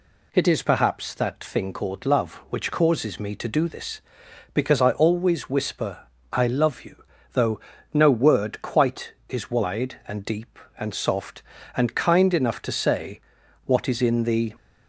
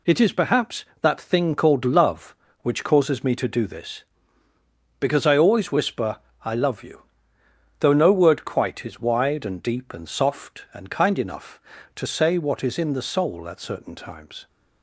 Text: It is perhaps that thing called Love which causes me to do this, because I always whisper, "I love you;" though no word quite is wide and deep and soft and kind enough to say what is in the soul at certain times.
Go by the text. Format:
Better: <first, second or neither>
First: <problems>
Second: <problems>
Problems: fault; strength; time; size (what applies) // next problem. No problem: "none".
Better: second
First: pauses between "though" and "no"; slight; at 7.5 s; 0.36 s long // pauses between "say" and "what"; at 13.2 s; 0.44 s long // stops before "soul at certain times"; at 14.5 s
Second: none